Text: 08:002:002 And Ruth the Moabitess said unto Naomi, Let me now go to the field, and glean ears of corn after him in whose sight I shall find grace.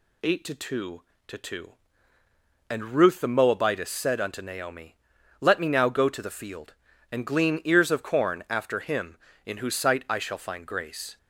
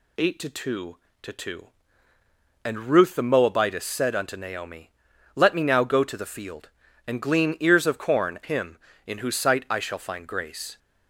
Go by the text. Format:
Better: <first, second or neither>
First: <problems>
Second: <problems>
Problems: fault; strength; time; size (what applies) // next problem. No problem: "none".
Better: first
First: none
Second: skips "after"; at 8.4 s